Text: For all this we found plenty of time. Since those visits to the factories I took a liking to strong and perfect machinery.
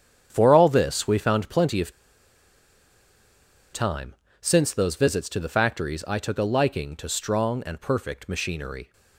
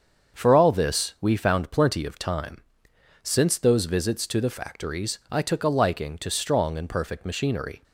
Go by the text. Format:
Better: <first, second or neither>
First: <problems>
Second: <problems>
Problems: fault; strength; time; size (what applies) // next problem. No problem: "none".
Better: second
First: starts louder than the rest; strong; until 1.3 s; 8 dB // pauses between "of" and "time"; strong; at 1.9 s; 1.8 s long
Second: starts louder than the rest; until 1.4 s; 7 dB